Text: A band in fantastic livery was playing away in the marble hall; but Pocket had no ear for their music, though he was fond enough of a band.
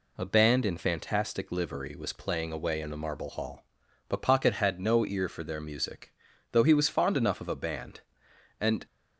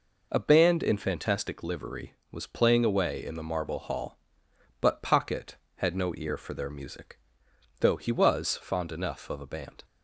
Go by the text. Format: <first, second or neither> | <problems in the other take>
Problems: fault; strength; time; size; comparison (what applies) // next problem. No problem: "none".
second | goes on to say "And"; slight; from 8.5 s on; 0.26 s long